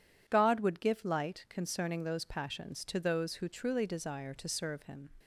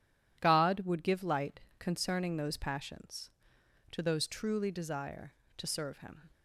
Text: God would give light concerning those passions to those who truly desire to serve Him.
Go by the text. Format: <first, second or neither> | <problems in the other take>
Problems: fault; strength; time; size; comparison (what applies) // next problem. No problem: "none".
first | pauses between "light" and "concerning"; slight; at 1.5 s; 0.20 s long // skips "who"; at 4.2 s